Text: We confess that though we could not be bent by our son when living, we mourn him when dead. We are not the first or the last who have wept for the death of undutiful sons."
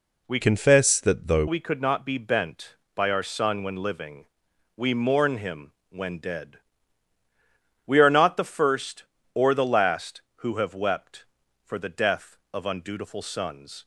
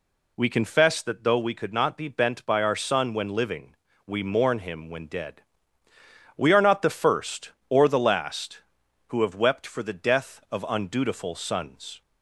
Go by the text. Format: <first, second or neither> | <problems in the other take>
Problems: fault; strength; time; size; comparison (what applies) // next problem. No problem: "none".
second | changes voice from "confess" to "though"; from 0.4 to 1.4 s; 1.0 s long // pauses between "him" and "when"; slight; at 5.7 s; 0.18 s long